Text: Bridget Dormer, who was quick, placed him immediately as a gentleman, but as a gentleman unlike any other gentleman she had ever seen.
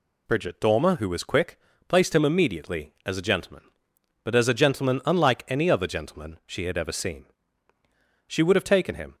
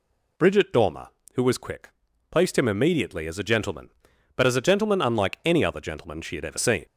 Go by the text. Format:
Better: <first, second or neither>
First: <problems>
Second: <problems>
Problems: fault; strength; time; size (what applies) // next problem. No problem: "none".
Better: second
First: goes on to say "She would have taken him"; noticeable; from 8.2 s on; 0.88 s long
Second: none